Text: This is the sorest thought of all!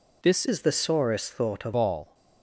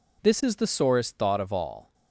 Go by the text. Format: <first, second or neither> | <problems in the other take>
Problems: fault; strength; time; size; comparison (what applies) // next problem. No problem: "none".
second | changes voice from "is" to "of"; from 0.4 to 1.7 s; 1.3 s long